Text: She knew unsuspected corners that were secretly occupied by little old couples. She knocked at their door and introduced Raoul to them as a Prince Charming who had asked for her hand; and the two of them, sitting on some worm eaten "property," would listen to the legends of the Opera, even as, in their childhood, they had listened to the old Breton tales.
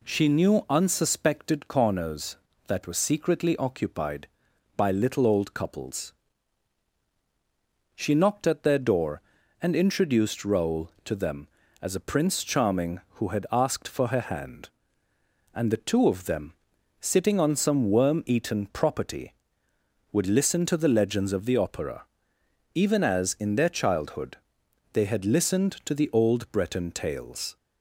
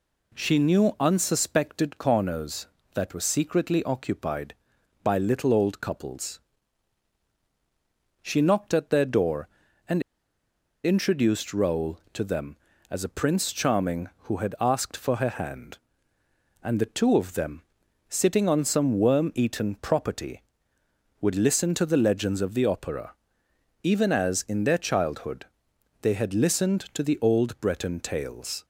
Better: first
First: none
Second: pauses between "and" and "introduced"; noticeable; at 10.0 s; 0.83 s long

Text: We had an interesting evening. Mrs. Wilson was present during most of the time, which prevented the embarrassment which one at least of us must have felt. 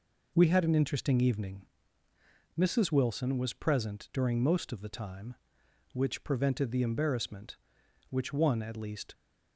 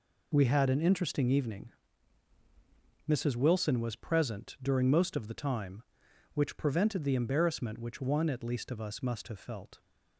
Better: second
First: stops before "of us must have felt"; at 9.1 s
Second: none

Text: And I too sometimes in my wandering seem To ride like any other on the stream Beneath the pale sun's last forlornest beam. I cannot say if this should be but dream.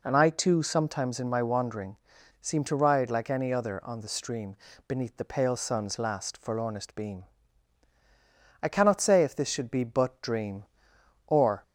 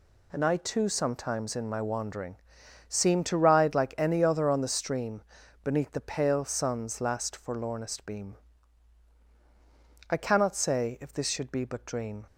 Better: second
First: pauses between "wandering" and "seem"; at 1.9 s; 0.44 s long // pauses between "stream" and "Beneath"; slight; at 4.5 s; 0.32 s long // goes on to say "Or"; slight; from 11.2 s on; 0.34 s long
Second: pauses between "wandering" and "seem"; noticeable; at 2.3 s; 0.52 s long // pauses between "stream" and "Beneath"; at 5.2 s; 0.42 s long

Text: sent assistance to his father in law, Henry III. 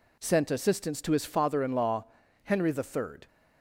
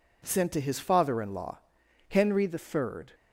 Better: first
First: none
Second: skips "assistance"; at 0.5 s

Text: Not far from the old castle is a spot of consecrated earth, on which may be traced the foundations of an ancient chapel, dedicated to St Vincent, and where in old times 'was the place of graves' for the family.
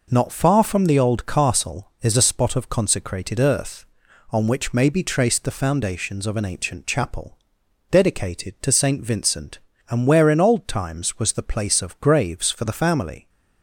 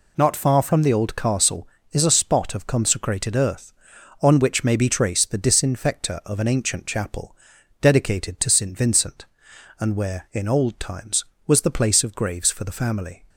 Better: first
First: none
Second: says "disinfector" for "foundations"; at 5.3 s

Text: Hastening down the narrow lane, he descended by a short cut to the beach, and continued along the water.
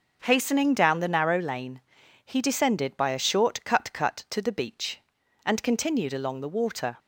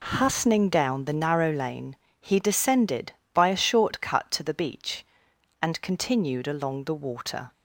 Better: second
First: says "cut" twice; at 3.9 s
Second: none

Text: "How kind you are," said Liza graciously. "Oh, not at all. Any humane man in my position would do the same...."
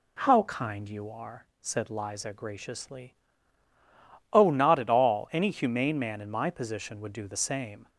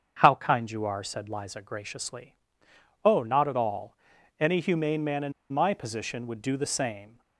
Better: first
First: none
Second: starts louder than the rest; strong; until 1.2 s; 7 dB // pauses between "in" and "my"; slight; at 5.3 s; 0.20 s long

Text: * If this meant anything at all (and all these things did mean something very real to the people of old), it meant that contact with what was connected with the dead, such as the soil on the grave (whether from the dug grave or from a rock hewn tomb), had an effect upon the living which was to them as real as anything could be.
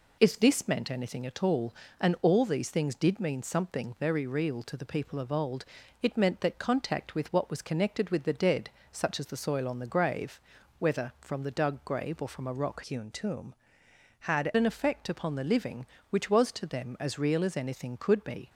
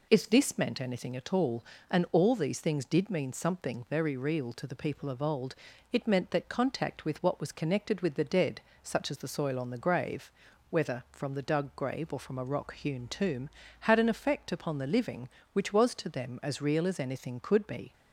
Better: second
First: changes voice from "hewn" to "had"; from 12.8 to 14.4 s; 1.6 s long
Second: none

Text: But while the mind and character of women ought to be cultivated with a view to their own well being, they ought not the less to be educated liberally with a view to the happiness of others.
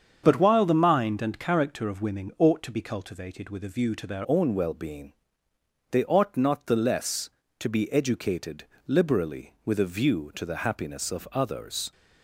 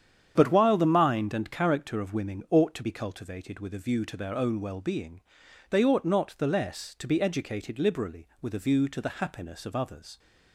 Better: second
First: starts louder than the rest; strong; until 1.2 s; 7.5 dB // changes voice at "own"; from 4.2 s on; 7.7 s long // pauses between "educated" and "liberally"; slight; at 8.6 s; 0.20 s long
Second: starts louder than the rest; strong; until 1.3 s; 8.5 dB

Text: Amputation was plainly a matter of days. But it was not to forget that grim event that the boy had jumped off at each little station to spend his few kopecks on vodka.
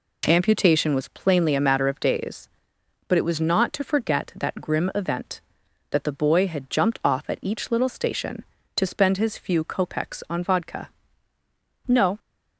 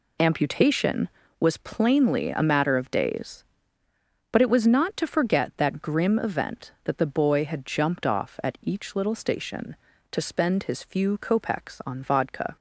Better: second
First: goes on to say "No"; slight; from 11.8 s on; 0.32 s long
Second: none

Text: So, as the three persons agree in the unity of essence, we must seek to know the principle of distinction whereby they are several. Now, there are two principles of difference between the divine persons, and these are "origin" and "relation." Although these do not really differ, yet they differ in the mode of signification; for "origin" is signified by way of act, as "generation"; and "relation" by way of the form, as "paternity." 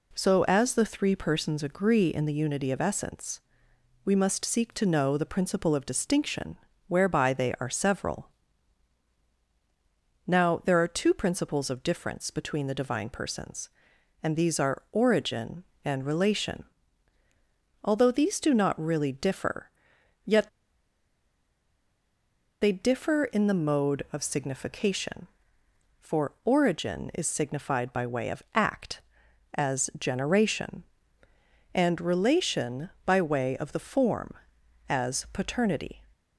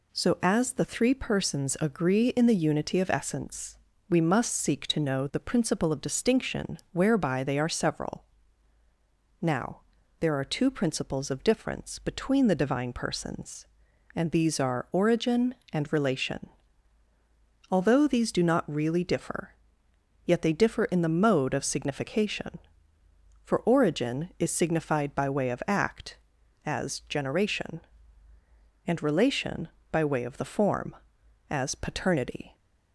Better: second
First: pauses between "distinction" and "whereby"; slight; at 6.5 s; 0.30 s long // pauses between "yet" and "they"; strong; at 20.4 s; 2.1 s long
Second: pauses between "distinction" and "whereby"; slight; at 6.7 s; 0.16 s long

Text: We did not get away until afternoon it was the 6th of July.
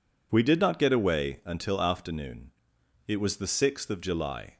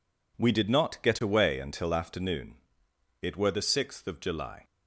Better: first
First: pauses between "afternoon" and "it"; noticeable; at 2.5 s; 0.56 s long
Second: pauses between "afternoon" and "it"; noticeable; at 2.5 s; 0.66 s long // says "were" for "was"; at 3.3 s

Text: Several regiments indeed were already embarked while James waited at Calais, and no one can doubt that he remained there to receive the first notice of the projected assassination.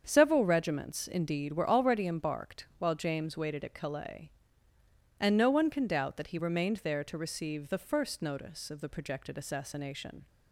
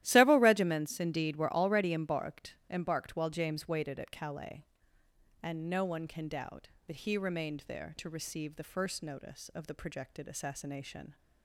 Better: first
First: starts louder than the rest; strong; until 1.0 s; 7.5 dB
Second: starts louder than the rest; strong; until 1.0 s; 13.5 dB // says "embarked" twice; at 2.7 s

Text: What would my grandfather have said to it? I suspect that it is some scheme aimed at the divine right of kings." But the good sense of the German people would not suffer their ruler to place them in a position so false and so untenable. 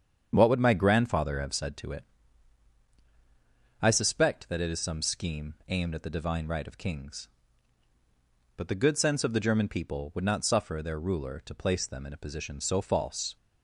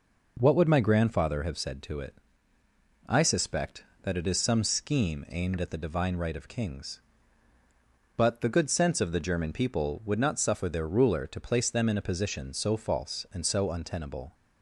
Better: second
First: starts louder than the rest; strong; until 1.3 s; 8 dB // stops before "and so untenable"; at 13.3 s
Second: none

